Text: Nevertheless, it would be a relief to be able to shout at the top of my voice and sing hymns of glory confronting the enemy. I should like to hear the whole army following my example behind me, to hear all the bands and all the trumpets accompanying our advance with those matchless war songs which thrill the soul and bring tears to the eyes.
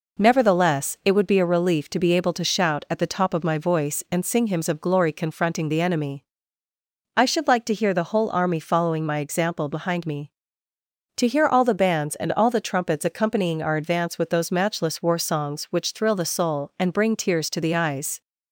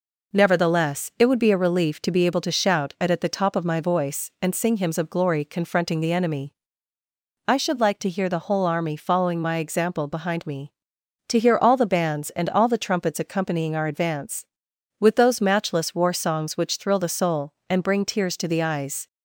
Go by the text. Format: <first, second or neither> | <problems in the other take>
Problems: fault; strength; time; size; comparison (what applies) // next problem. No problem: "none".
first | says "at" twice; at 3.1 s